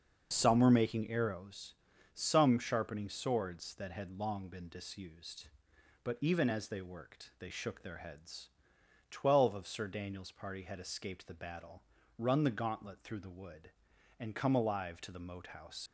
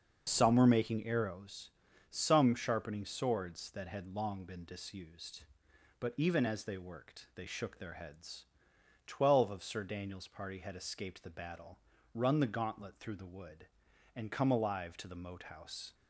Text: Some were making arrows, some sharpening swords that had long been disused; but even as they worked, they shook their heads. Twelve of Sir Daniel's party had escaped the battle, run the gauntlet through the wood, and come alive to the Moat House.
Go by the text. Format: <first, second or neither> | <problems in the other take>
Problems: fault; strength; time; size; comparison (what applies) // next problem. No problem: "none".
second | starts louder than the rest; until 1.3 s; 6 dB; also in the second // leaves "House" unfinished; at 15.8 s; 115 ms